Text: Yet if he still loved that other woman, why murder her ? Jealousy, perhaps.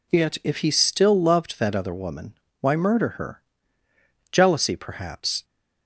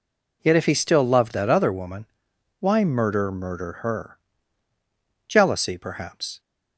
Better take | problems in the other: first | says "murder" twice; at 3.2 s

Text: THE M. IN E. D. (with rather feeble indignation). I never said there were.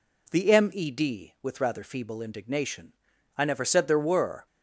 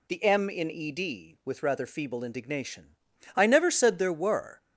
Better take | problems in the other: second | skips "IN"; at 0.7 s

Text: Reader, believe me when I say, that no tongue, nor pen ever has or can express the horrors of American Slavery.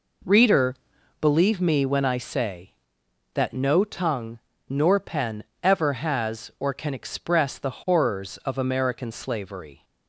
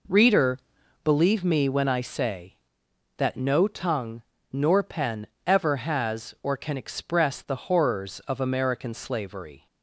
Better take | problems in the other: neither | pauses between "pen" and "ever"; slight; the same in both

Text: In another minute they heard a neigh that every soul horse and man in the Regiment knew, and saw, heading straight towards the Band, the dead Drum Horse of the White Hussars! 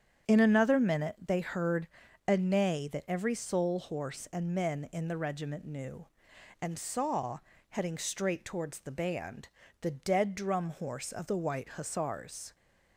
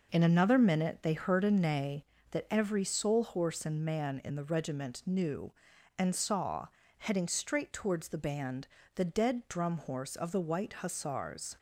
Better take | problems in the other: second | starts louder than the rest; strong; until 1.3 s; 8.5 dB // pauses between "heard" and "a"; at 1.8 s; 0.40 s long // says "men" for "man"; at 4.5 s

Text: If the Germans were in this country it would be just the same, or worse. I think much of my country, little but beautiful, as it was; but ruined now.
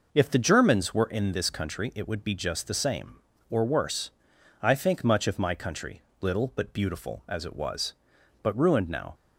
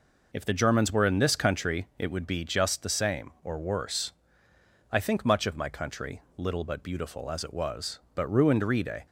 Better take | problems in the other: first | says "rede" for "now"; at 8.6 s

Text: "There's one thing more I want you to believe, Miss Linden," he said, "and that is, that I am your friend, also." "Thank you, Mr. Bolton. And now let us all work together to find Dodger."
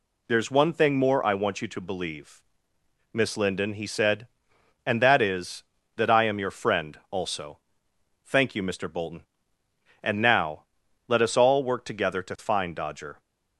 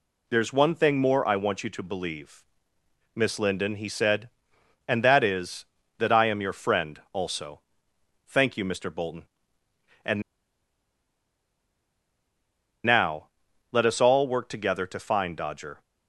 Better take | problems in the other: first | pauses between "And" and "now"; strong; at 10.2 s; 2.6 s long // pauses between "now" and "let"; at 13.2 s; 0.44 s long; also in the first

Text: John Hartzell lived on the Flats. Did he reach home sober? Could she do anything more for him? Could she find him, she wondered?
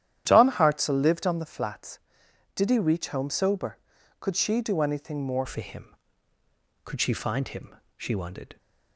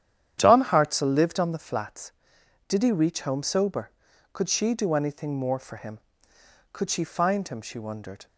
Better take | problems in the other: second | starts louder than the rest; strong; until 1.2 s; 11 dB; strong in the second // changes voice at "for"; from 5.4 s on; 3.1 s long

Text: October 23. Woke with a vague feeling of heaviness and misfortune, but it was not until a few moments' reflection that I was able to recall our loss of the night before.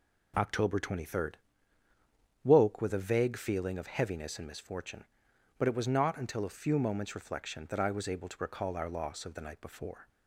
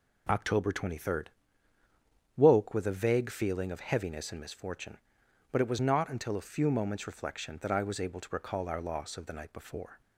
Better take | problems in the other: neither | none

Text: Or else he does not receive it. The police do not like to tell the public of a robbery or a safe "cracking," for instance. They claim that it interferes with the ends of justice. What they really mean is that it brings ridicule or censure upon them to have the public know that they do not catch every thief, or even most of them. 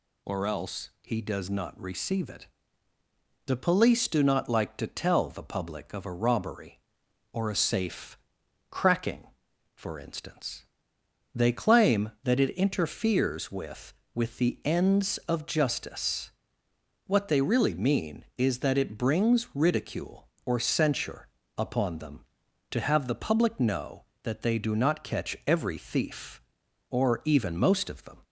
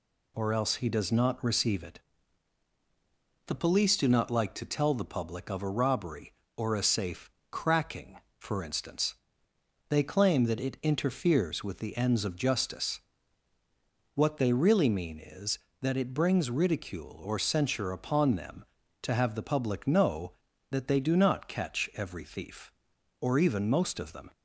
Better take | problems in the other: second | pauses between "safe" and "cracking"; noticeable; at 8.1 s; 0.52 s long; slight in the second // says "with" twice; at 14.1 s // pauses between "censure" and "upon"; slight; at 21.2 s; 0.30 s long

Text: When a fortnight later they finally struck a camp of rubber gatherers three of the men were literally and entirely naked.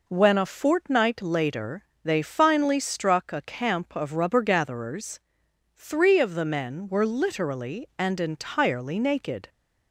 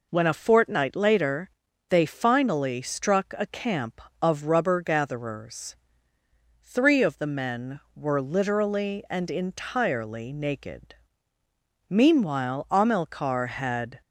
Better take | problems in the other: first | pauses between "later" and "they"; at 1.5 s; 0.40 s long; slight in the first // pauses between "gatherers" and "three"; noticeable; at 5.7 s; 0.90 s long; noticeable in the first // goes on to say "Meanwhile Amilcar had"; strong; from 11.9 s on; 2.1 s long

